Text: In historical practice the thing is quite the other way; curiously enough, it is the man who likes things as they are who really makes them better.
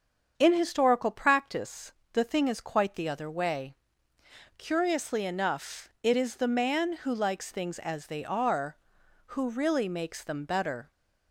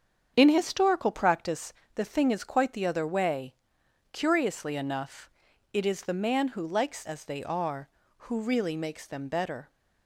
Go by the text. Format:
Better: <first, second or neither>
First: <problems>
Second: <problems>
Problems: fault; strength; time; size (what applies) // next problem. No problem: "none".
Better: first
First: starts louder than the rest; strong; until 1.3 s; 7 dB // pauses between "practice" and "the"; slight; at 1.9 s; 0.18 s long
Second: starts louder than the rest; strong; until 1.3 s; 7.5 dB // pauses between "practice" and "the"; slight; at 1.7 s; 0.22 s long // skips "things"; at 7.0 s